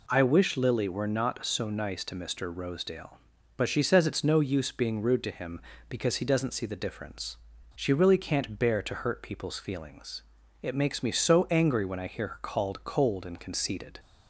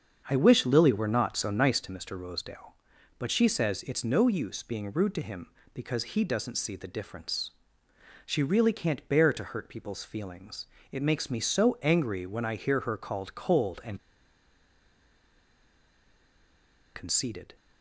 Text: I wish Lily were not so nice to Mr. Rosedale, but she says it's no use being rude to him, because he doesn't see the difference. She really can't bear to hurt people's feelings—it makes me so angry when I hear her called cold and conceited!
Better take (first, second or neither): first